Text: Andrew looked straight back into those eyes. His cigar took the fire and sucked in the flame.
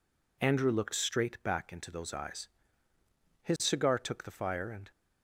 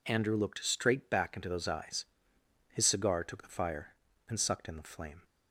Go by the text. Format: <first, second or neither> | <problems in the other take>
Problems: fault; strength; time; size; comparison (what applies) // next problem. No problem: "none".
second | stops before "sucked in the flame"; at 4.9 s